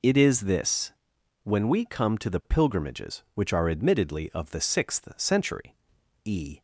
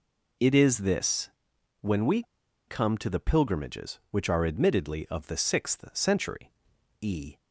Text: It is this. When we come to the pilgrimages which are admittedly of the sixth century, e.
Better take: first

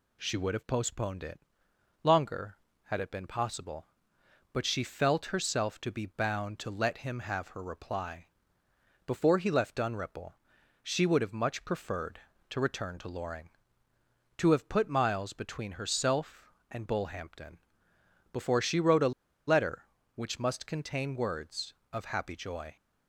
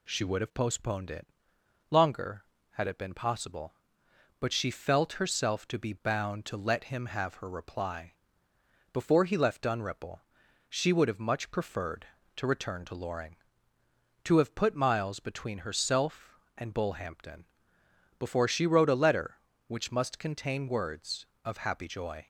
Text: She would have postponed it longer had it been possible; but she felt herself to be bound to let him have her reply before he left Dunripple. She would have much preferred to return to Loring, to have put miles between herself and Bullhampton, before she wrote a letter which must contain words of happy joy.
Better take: second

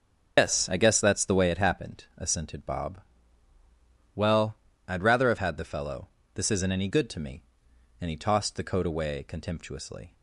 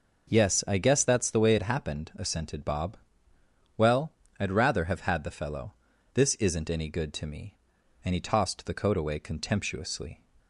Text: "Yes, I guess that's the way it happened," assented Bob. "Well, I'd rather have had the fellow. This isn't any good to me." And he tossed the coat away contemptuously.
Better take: second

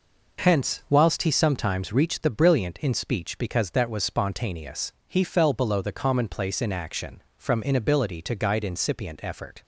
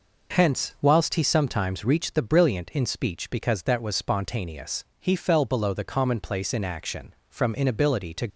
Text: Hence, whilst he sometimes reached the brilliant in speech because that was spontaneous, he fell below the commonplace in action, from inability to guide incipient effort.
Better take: first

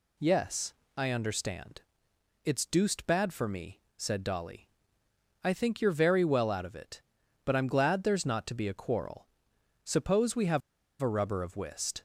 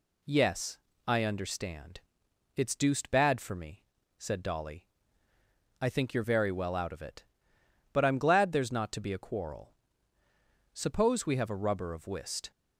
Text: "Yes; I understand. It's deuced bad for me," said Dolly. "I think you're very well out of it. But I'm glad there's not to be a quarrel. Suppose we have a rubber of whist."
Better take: second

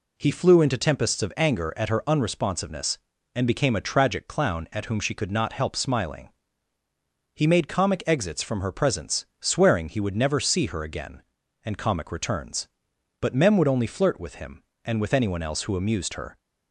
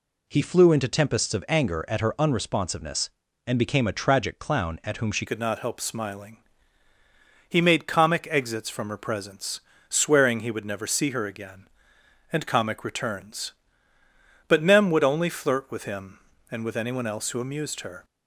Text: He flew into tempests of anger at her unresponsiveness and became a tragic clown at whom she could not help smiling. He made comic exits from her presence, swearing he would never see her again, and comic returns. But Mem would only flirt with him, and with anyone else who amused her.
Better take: first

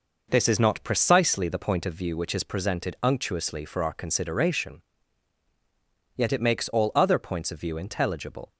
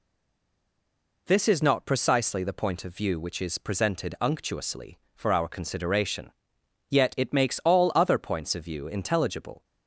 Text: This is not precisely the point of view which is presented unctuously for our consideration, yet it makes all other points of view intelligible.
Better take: first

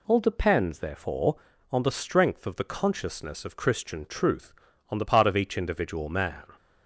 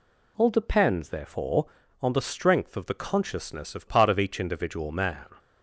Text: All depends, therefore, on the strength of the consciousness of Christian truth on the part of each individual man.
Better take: first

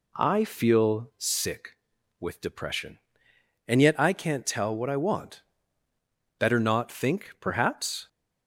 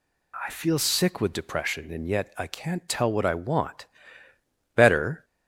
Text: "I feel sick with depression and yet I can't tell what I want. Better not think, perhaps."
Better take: first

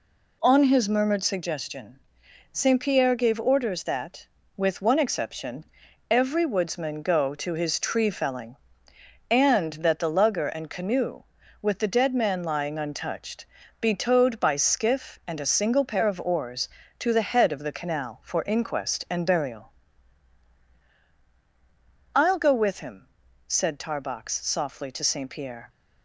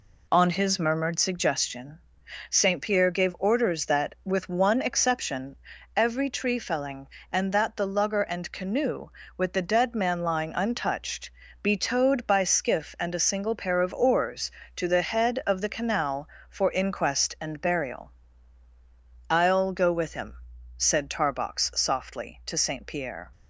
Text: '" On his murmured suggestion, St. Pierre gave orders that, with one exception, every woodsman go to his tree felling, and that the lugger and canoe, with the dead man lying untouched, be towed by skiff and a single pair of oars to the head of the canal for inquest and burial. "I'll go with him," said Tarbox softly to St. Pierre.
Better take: first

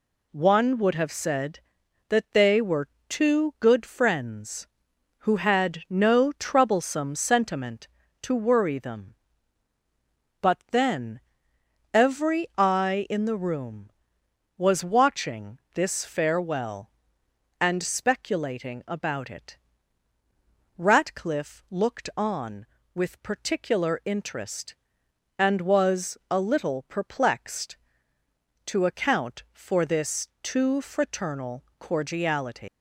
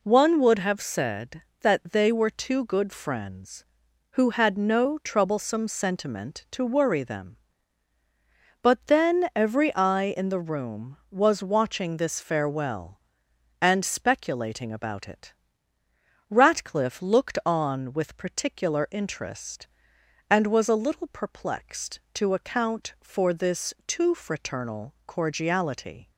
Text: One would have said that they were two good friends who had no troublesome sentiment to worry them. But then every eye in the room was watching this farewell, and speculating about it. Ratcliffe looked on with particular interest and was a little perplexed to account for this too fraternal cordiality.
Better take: second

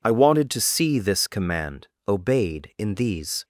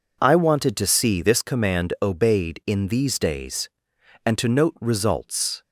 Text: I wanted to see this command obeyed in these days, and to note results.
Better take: second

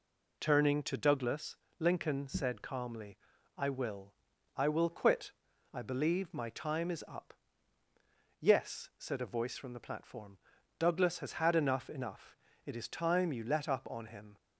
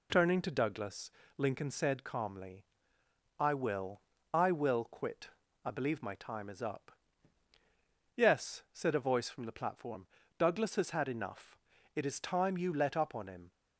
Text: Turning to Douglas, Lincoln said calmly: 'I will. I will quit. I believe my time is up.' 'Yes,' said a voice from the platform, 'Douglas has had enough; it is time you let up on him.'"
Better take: second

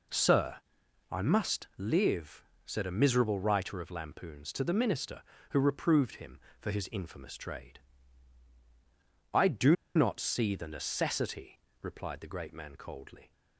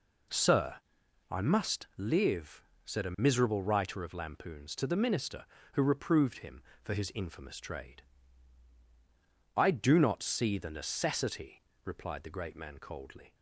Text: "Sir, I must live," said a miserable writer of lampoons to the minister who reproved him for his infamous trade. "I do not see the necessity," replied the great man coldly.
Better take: second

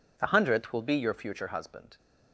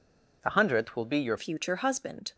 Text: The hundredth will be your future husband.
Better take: first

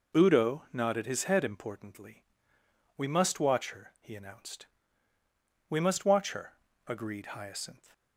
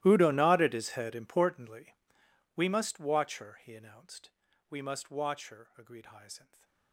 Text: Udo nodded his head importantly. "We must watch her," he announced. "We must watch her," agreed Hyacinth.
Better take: first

